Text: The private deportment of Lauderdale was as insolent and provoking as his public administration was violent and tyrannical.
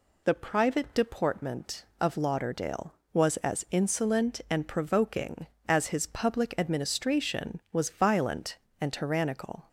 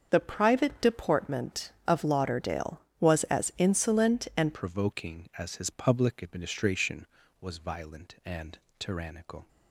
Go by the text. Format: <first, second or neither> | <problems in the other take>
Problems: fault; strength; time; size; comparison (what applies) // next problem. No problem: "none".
first | starts louder than the rest; until 1.1 s; 6.5 dB // changes voice at "provoking"; from 4.5 s on; 4.9 s long // pauses between "and" and "tyrannical"; slight; at 8.5 s; 0.20 s long